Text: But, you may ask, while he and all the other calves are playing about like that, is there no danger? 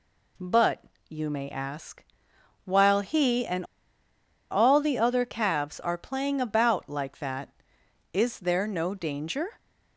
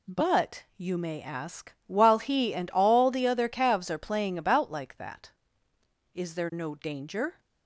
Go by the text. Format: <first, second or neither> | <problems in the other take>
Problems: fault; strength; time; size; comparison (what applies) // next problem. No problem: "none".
second | pauses between "and" and "all"; noticeable; at 3.6 s; 0.86 s long